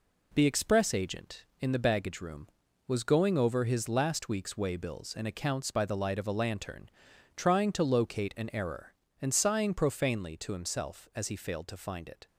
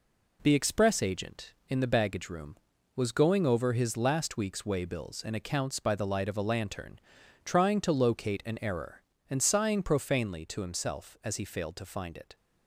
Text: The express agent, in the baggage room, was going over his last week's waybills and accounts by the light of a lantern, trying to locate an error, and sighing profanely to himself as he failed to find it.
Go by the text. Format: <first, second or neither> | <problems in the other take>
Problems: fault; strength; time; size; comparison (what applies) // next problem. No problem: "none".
neither | none